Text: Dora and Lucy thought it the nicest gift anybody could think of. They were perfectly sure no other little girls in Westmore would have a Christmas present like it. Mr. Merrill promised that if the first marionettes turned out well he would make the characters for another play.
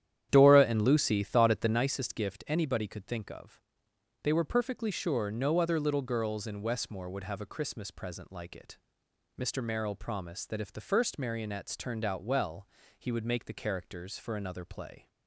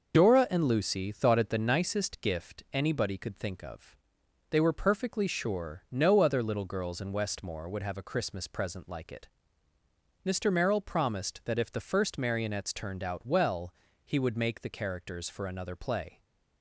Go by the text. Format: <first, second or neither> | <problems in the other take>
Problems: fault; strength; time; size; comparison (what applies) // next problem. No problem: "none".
second | starts louder than the rest; strong; until 1.8 s; 10.5 dB // pauses between "well" and "he"; slight; at 12.6 s; 0.30 s long; slight in the second